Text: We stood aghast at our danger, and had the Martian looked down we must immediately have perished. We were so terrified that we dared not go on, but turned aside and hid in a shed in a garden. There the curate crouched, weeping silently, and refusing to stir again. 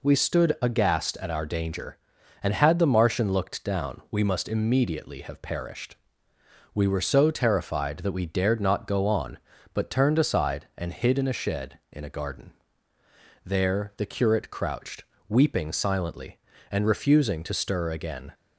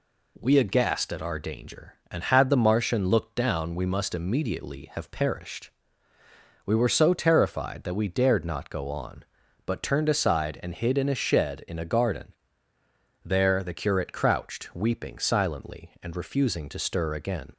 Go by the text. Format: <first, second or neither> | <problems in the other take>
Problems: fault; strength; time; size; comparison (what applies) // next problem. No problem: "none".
first | skips "stood"; at 0.5 s